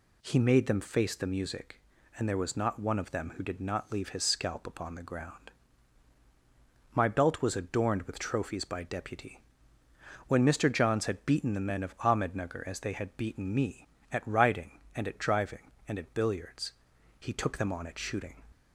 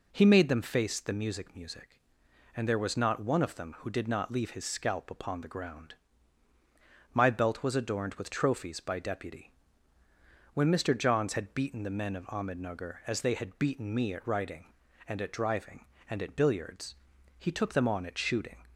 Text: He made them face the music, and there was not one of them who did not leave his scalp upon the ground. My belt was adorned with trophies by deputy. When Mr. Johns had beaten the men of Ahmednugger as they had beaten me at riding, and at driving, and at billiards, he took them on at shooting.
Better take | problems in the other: first | says "music" twice; at 1.5 s

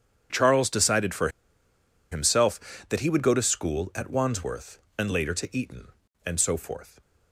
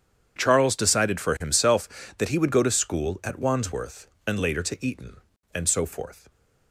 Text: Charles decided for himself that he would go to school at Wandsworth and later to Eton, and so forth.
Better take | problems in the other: second | starts louder than the rest; strong; until 2.1 s; 8 dB; strong in the second // pauses between "for" and "himself"; noticeable; at 1.2 s; 0.82 s long

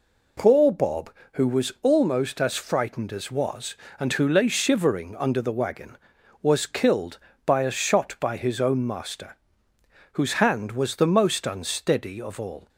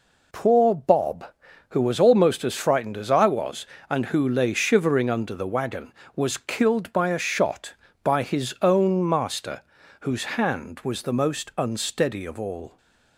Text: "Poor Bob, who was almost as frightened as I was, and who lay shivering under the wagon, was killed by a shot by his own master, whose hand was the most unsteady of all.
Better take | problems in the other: second | skips "I"; at 3.2 s

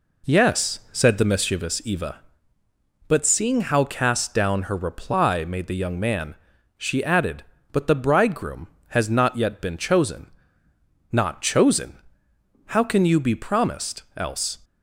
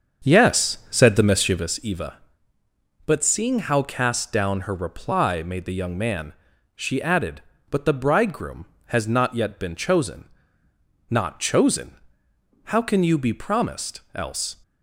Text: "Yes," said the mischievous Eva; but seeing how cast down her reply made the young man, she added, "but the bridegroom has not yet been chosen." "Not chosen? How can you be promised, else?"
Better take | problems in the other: first | starts louder than the rest; until 1.8 s; 7 dB

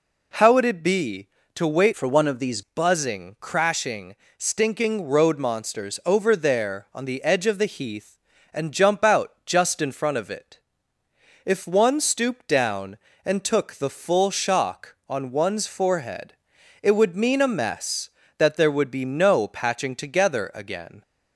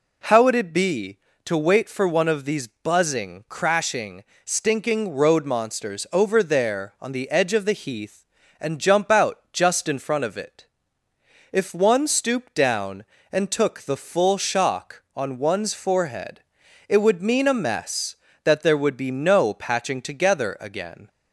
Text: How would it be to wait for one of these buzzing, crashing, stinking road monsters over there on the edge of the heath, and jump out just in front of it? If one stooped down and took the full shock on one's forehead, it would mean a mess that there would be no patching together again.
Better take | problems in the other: second | changes voice from "for" to "these"; from 1.9 to 2.6 s; 0.7 s long

